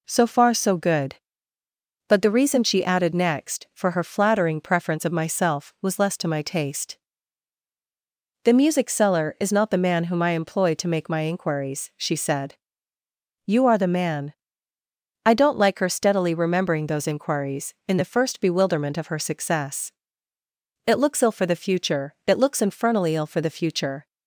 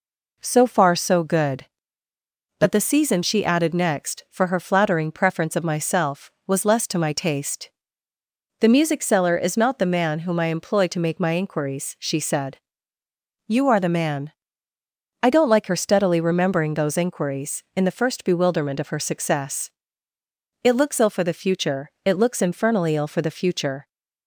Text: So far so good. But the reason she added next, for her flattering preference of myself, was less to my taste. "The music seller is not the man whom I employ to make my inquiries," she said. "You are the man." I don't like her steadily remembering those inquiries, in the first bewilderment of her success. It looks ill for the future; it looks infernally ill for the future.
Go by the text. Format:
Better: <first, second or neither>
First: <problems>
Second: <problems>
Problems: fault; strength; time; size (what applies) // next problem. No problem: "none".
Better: first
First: none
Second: says "season" for "reason"; at 2.7 s